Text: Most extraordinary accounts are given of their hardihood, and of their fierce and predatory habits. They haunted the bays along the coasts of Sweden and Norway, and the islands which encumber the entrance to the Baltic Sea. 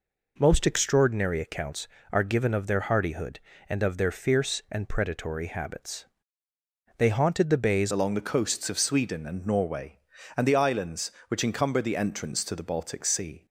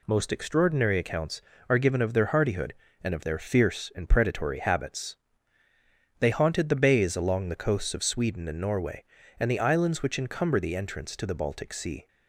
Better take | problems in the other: second | changes voice at "along"; from 7.9 s on; 5.5 s long

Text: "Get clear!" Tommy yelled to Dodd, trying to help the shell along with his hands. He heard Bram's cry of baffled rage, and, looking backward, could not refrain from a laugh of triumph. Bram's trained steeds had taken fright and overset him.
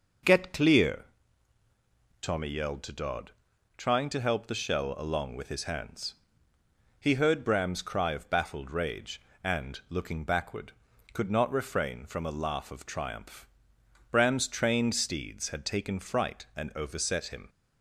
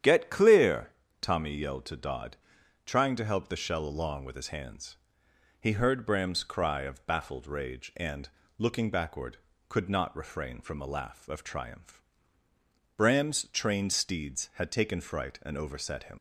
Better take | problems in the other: first | starts louder than the rest; strong; until 1.3 s; 9.5 dB // leaves "him" unfinished; at 16.1 s; 70 ms

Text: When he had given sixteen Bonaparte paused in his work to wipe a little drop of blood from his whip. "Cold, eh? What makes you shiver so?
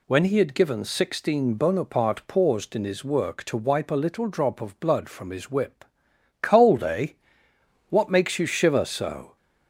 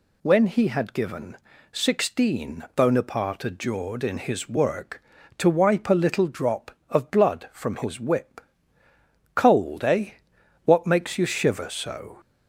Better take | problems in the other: first | pauses between "given" and "sixteen"; slight; at 1.3 s; 0.34 s long // says "adjured" for "paused"; at 3.4 s

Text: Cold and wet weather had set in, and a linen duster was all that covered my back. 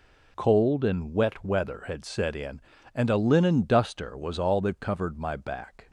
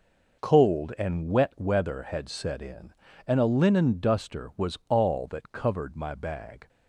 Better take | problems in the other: first | says "bag" for "back"; at 6.1 s

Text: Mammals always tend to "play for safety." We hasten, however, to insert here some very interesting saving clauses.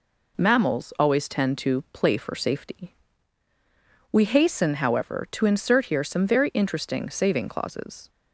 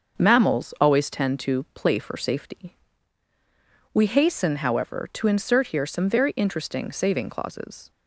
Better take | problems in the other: first | starts louder than the rest; until 1.2 s; 6.5 dB

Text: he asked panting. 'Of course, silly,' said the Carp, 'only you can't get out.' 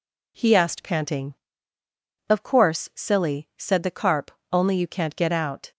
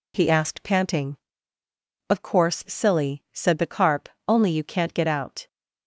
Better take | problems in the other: neither | none

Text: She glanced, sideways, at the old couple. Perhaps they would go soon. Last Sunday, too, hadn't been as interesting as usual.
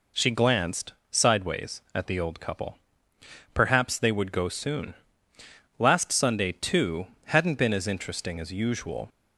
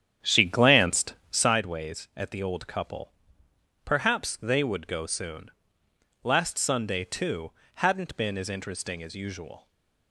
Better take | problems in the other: first | starts louder than the rest; strong; until 1.6 s; 9.5 dB // stays silent after the last word; slight; from 9.5 s on; 0.6 s long

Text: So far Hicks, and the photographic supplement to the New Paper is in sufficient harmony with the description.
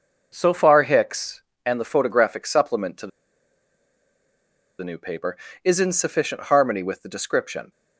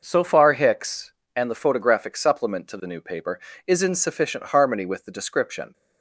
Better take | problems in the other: second | pauses between "the" and "New"; strong; at 3.1 s; 1.7 s long

